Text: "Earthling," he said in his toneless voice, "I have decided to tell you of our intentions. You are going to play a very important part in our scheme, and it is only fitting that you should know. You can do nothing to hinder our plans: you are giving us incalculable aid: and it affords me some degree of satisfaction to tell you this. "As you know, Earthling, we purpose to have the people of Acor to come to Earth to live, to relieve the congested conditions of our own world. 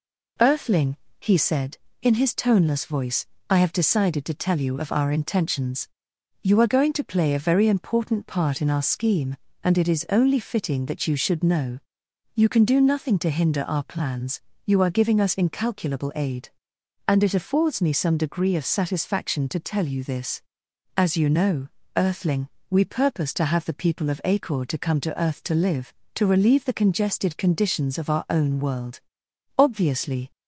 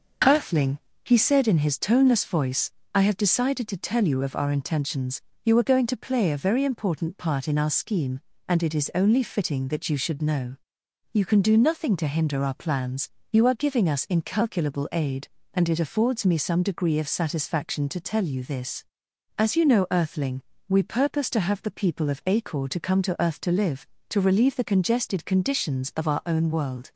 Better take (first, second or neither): second